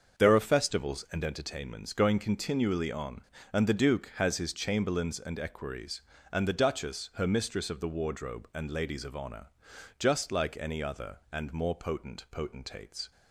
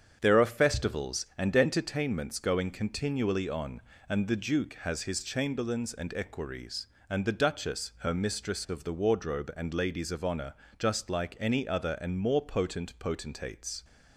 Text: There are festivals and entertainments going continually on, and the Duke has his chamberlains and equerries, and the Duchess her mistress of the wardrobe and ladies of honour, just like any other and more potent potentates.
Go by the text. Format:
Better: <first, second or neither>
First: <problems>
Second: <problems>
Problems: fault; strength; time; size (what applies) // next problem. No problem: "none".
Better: neither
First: starts louder than the rest; until 1.2 s; 6.5 dB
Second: starts louder than the rest; strong; until 1.2 s; 8 dB